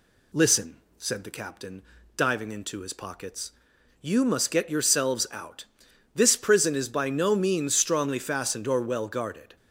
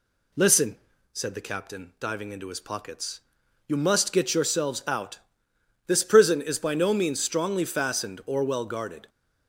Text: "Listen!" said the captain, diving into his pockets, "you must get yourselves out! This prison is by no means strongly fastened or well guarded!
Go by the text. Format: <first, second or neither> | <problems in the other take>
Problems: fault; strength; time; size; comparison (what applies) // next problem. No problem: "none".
neither | none